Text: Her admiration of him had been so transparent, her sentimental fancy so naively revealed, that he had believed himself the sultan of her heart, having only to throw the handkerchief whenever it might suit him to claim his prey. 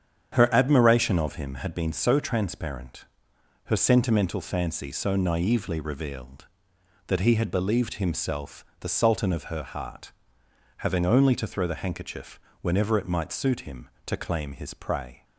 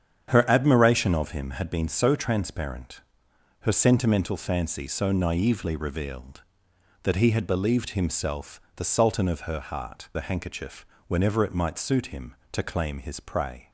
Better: first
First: starts louder than the rest; strong; until 1.3 s; 8.5 dB // pauses between "handkerchief" and "whenever"; slight; at 12.4 s; 0.22 s long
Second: starts louder than the rest; strong; until 1.3 s; 8.5 dB // skips "having only to throw"; at 10.1 s // pauses between "handkerchief" and "whenever"; slight; at 10.8 s; 0.22 s long

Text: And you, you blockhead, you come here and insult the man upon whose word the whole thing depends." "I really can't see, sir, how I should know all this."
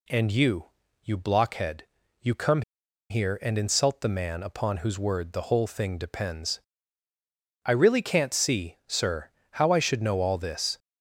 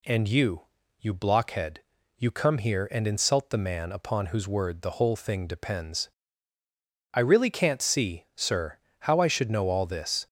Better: second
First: pauses between "come" and "here"; noticeable; at 2.6 s; 0.47 s long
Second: none

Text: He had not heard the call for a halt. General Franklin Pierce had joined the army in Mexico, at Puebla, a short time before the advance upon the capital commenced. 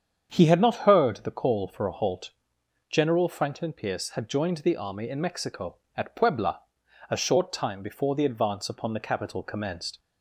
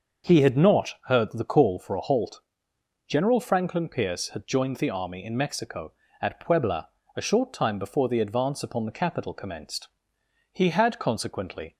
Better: first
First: starts louder than the rest; strong; until 1.3 s; 7.5 dB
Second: starts louder than the rest; until 1.3 s; 6 dB // goes on to say "He had consequently"; noticeable; from 10.5 s on; 1.2 s long

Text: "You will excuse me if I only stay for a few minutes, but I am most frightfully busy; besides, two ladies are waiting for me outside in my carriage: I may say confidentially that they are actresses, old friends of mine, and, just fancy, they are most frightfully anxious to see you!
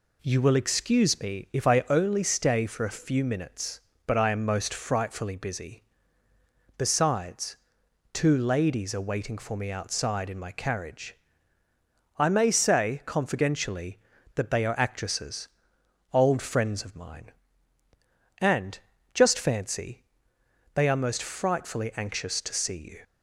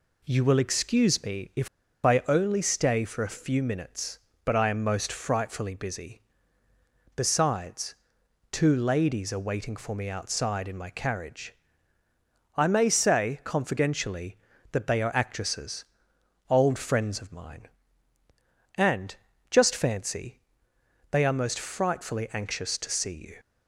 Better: first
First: none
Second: pauses between "if" and "I"; slight; at 1.6 s; 0.35 s long

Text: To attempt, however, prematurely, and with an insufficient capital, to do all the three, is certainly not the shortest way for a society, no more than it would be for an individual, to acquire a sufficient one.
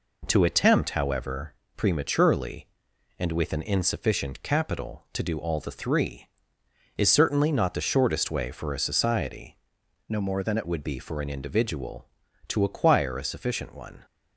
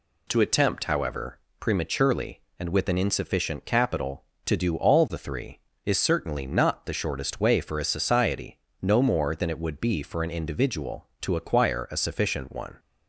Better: second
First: changes voice from "no" to "it"; from 10.0 to 10.6 s; 0.6 s long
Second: none

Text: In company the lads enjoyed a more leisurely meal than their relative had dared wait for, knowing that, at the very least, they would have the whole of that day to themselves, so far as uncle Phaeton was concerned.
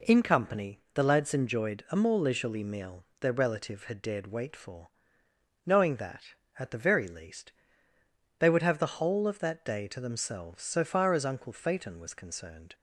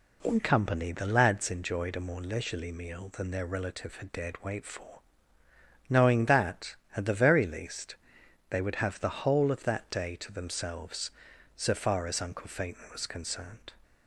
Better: second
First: pauses between "company" and "the"; slight; at 0.7 s; 0.16 s long // skips "than"; at 3.1 s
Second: none

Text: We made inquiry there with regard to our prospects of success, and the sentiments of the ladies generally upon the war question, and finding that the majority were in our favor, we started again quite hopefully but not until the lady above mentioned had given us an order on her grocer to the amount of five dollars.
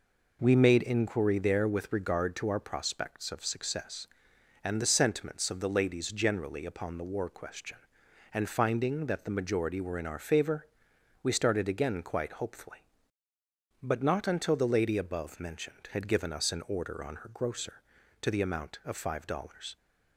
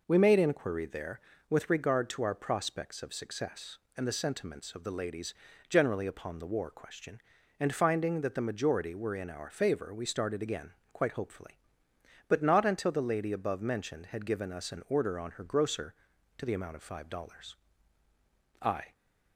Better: first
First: none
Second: pauses between "ladies" and "generally"; slight; at 5.3 s; 0.36 s long // pauses between "again" and "quite"; slight; at 10.7 s; 0.20 s long // goes on to say "I"; slight; from 18.6 s on; 0.32 s long

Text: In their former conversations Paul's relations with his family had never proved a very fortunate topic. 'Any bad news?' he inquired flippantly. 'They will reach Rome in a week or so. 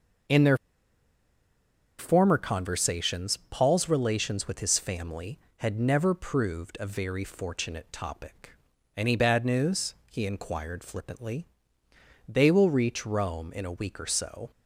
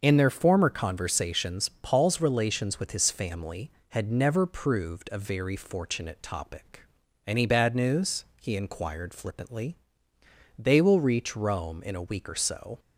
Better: second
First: pauses between "their" and "former"; strong; at 0.5 s; 1.4 s long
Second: none

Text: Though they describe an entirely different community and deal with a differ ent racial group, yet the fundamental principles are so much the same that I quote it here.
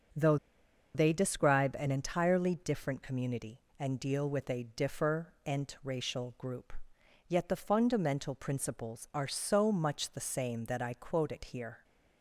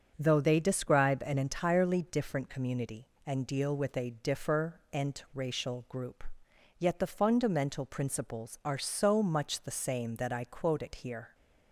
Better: second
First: starts louder than the rest; until 1.7 s; 6.5 dB // pauses between "Though" and "they"; noticeable; at 0.3 s; 0.59 s long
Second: starts louder than the rest; until 1.1 s; 6.5 dB

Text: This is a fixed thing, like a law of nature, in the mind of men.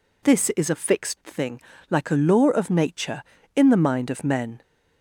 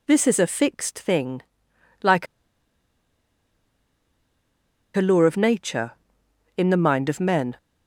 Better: first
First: none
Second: pauses between "like" and "a"; strong; at 2.2 s; 2.6 s long

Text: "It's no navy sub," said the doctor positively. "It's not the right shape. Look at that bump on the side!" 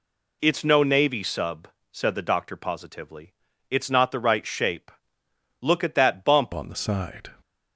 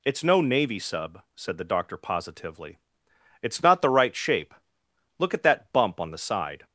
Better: second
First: changes voice at "on"; from 6.5 s on; 0.8 s long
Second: none

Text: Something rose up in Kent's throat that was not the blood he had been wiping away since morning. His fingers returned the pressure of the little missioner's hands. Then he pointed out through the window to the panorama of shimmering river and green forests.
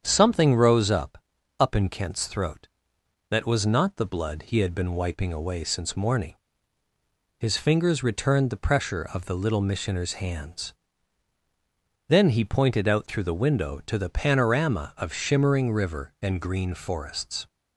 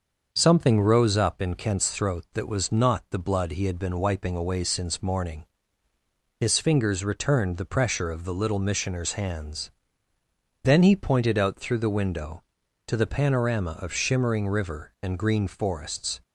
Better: second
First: starts louder than the rest; strong; until 1.0 s; 8 dB // says "up" twice; at 1.6 s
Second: starts louder than the rest; until 1.3 s; 6.5 dB

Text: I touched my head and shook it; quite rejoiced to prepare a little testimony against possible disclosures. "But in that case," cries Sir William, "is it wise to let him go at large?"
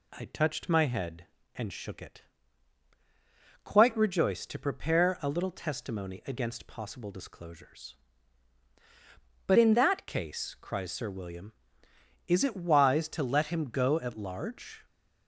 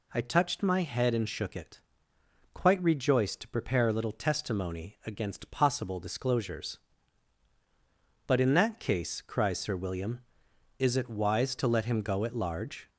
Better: second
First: changes voice from "in" to "that"; from 9.5 to 10.0 s; 0.5 s long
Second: none

